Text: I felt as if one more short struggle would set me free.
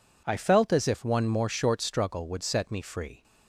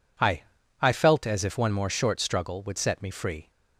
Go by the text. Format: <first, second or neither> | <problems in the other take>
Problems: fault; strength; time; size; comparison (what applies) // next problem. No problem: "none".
first | says "I" twice; at 0.8 s